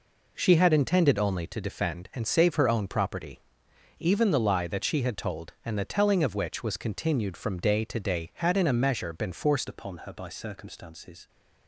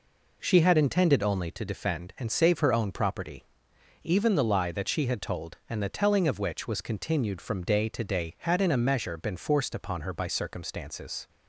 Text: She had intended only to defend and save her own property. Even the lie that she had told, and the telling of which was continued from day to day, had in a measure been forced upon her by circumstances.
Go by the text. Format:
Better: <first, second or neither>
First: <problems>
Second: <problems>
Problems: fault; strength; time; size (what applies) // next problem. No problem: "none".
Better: second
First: changes voice at "upon"; from 9.6 s on; 1.6 s long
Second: none